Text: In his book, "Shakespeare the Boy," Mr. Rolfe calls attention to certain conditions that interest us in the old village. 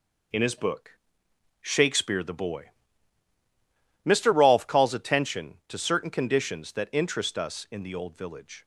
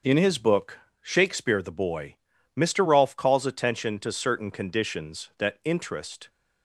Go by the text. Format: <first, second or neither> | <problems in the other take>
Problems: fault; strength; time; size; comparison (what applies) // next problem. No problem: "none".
first | starts louder than the rest; until 1.2 s; 6.5 dB // stops before "us in the old village"; at 6.2 s